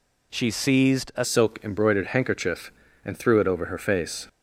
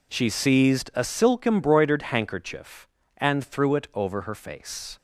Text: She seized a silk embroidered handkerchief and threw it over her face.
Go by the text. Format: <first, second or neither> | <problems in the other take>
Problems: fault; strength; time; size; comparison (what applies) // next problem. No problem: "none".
second | changes voice at "silk"; from 1.2 s on; 3.0 s long